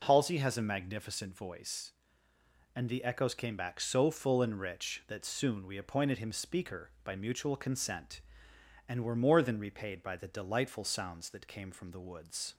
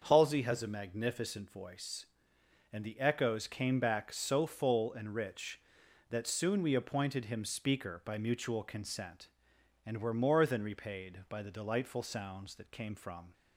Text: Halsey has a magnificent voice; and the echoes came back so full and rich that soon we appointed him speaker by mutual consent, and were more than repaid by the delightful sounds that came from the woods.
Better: first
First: none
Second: starts louder than the rest; until 1.0 s; 6.5 dB // stops before "the woods"; at 13.3 s

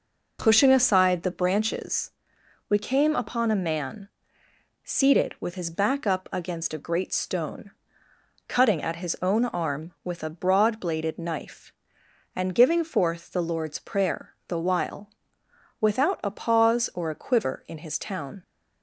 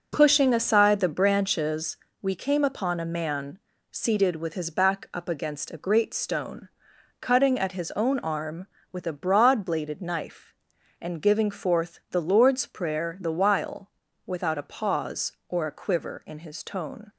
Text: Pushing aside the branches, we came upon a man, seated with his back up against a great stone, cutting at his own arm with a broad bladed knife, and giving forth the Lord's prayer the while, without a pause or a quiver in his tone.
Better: second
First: pauses between "prayer" and "the"; slight; at 14.3 s; 0.18 s long // says "town" for "tone"; at 17.9 s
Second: none

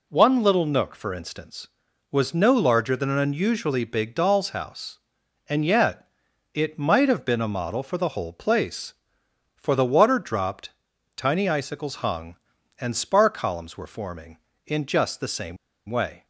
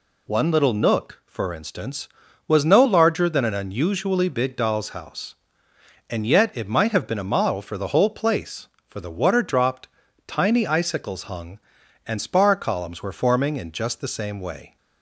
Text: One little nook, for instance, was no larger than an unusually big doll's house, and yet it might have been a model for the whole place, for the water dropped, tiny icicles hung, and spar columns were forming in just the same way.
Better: second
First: pauses between "yet" and "it"; noticeable; at 6.0 s; 0.46 s long // pauses between "same" and "way"; slight; at 15.5 s; 0.32 s long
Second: none

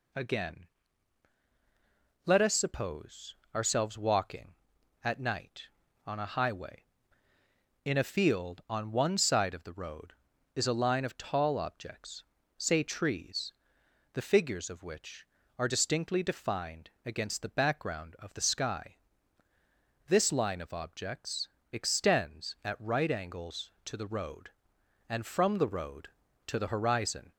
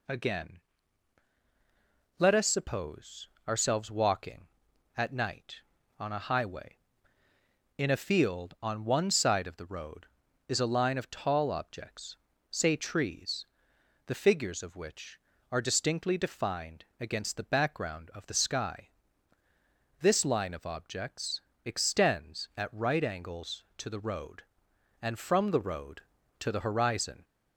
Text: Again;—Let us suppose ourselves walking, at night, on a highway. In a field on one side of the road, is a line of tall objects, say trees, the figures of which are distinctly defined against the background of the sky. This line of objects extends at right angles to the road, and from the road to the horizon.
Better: neither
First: pauses between "suppose" and "ourselves"; slight; at 3.3 s; 0.20 s long // pauses between "defined" and "against"; slight; at 16.8 s; 0.16 s long // pauses between "objects" and "extends"; slight; at 21.4 s; 0.22 s long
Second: pauses between "suppose" and "ourselves"; slight; at 3.2 s; 0.20 s long // pauses between "defined" and "against"; slight; at 16.8 s; 0.16 s long // pauses between "objects" and "extends"; slight; at 21.4 s; 0.22 s long

